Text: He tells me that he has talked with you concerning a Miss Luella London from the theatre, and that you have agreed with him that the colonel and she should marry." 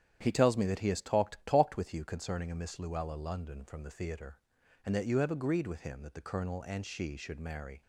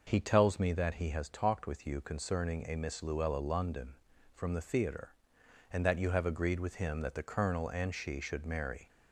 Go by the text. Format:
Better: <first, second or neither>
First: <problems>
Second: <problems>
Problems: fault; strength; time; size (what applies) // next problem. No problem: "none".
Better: second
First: starts louder than the rest; strong; until 1.2 s; 9.5 dB // says "talked" twice; at 1.4 s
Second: none